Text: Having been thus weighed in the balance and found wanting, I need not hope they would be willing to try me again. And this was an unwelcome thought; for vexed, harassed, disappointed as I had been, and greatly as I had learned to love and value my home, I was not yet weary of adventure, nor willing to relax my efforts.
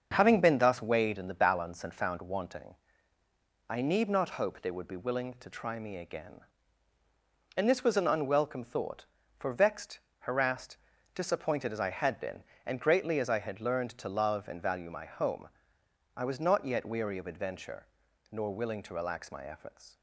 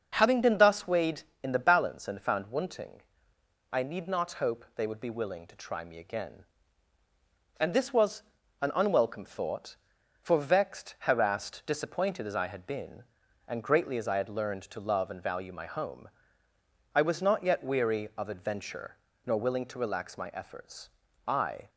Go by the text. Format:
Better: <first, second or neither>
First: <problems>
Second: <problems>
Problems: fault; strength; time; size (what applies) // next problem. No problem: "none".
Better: first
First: starts louder than the rest; until 1.1 s; 6.5 dB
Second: starts louder than the rest; noticeable; until 1.1 s; 6 dB // pauses between "was" and "an"; at 8.2 s; 0.40 s long // goes on to say "I"; slight; from 21.2 s on; 0.44 s long